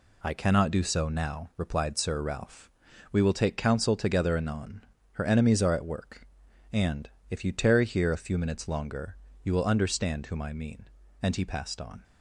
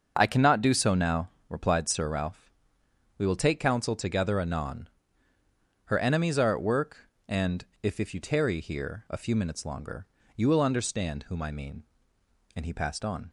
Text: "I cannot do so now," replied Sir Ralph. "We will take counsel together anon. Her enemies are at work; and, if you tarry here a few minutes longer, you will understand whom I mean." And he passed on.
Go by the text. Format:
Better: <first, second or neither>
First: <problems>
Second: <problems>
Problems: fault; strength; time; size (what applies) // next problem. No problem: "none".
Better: first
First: none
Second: starts louder than the rest; until 1.1 s; 6.5 dB // says "if" twice; at 8.0 s